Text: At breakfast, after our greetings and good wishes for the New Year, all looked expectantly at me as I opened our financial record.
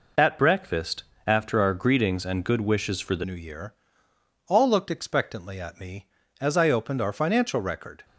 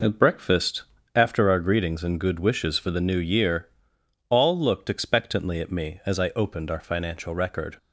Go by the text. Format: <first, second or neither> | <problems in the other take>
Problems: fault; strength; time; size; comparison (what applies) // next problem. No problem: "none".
second | changes voice at "New"; from 3.2 s on; 4.8 s long